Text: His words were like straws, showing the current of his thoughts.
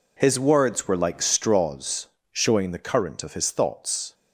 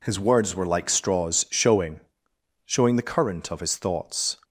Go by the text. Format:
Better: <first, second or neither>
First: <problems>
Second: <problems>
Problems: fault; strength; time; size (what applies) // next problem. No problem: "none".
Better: first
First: none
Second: says "showing" twice; at 2.6 s